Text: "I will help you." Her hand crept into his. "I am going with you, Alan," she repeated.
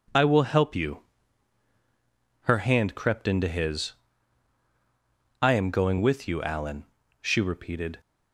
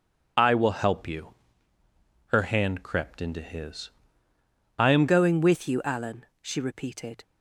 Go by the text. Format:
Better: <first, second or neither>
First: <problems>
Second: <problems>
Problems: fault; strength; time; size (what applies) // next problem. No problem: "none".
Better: first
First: none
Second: changes voice at "going"; from 5.0 s on; 2.2 s long